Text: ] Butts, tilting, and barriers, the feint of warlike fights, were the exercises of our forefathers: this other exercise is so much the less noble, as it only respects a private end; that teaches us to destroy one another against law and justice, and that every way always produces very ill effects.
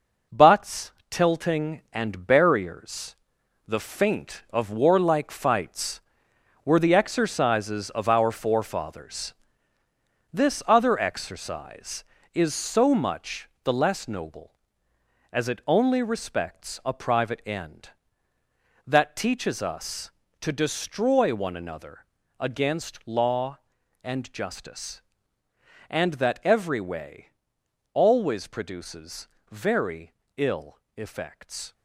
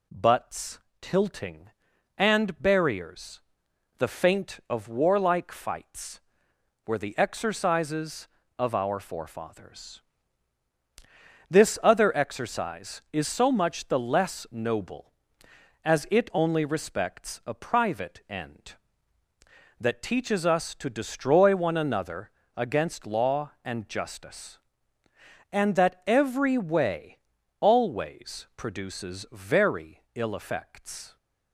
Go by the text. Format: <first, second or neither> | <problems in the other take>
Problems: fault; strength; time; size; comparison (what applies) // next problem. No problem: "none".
second | gets quieter; throughout; 6.5 dB // pauses between "another" and "against"; slight; at 22.0 s; 0.34 s long; slight in the second // pauses between "way" and "always"; noticeable; at 27.2 s; 0.66 s long; also in the second // pauses between "produces" and "very"; slight; at 29.2 s; 0.24 s long // pauses between "very" and "ill"; slight; at 30.1 s; 0.24 s long // pauses between "ill" and "effects"; slight; at 30.7 s; 0.16 s long